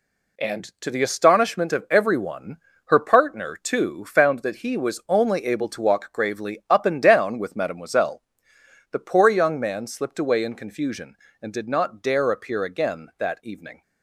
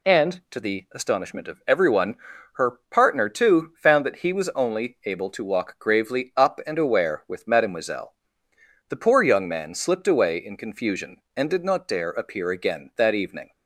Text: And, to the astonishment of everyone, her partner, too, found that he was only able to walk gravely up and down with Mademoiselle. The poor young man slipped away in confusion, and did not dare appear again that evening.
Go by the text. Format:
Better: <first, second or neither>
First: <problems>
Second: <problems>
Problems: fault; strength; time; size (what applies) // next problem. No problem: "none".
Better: first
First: none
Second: says "aware" for "down"; at 6.7 s